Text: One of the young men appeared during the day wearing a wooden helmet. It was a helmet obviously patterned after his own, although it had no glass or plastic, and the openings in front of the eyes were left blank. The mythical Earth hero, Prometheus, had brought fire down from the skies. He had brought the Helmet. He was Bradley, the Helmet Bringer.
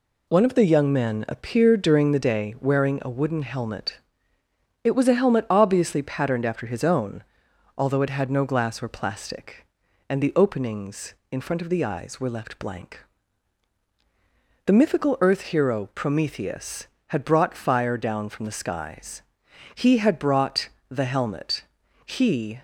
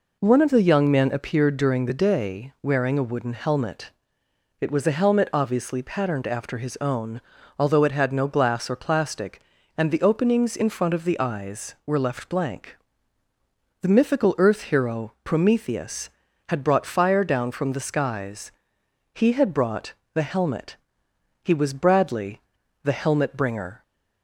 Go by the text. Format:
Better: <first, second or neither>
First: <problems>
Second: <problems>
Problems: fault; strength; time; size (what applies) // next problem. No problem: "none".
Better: second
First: pauses between "brought" and "the"; slight; at 20.6 s; 0.22 s long // stops before "was Bradley the Helmet Bringer"; at 22.5 s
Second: pauses between "brought" and "the"; slight; at 19.9 s; 0.22 s long